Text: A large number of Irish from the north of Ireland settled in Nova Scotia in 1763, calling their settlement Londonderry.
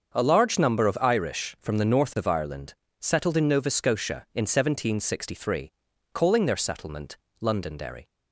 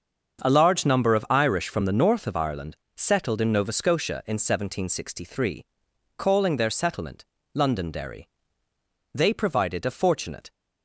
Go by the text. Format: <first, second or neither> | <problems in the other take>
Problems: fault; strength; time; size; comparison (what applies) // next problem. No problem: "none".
first | starts louder than the rest; until 1.4 s; 6.5 dB; also in the first // pauses between "Ireland" and "settled"; slight; at 2.7 s; 0.18 s long; slight in the first // pauses between "settlement" and "Londonderry"; slight; at 7.2 s; 0.28 s long; slight in the first // goes on to say "They provided a fortunate"; from 9.1 s on; 1.3 s long